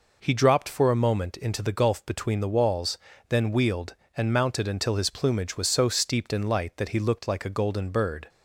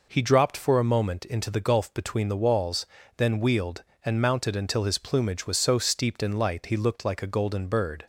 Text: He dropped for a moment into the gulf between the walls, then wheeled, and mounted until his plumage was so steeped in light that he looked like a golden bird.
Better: first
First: none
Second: skips "that"; at 6.6 s

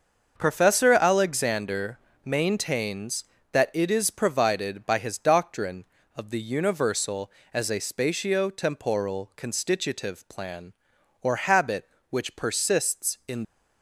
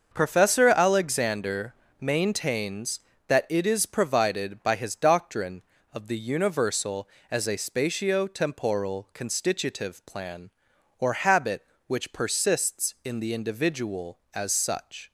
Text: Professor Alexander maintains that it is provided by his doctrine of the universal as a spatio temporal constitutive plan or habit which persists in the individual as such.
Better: second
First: starts louder than the rest; until 1.3 s; 6.5 dB // pauses between "Alexander" and "maintains"; slight; at 1.9 s; 0.28 s long // stops before "the individual as such"; at 13.4 s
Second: starts louder than the rest; until 1.1 s; 6.5 dB // pauses between "Alexander" and "maintains"; slight; at 1.7 s; 0.28 s long

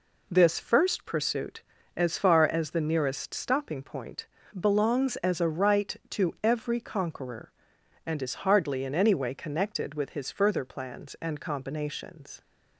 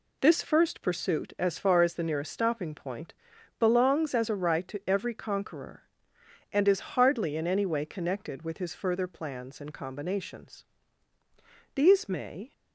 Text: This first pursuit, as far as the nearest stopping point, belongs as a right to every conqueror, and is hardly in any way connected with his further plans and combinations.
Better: first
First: none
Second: goes on to say "These may"; noticeable; from 11.7 s on; 0.78 s long

